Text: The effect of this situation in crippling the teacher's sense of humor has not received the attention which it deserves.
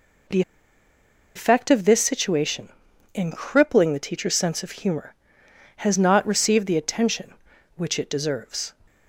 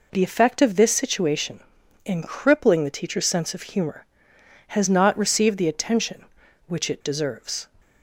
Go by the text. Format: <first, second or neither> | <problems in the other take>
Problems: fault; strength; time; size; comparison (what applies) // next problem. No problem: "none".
second | pauses between "The" and "effect"; noticeable; at 0.4 s; 0.94 s long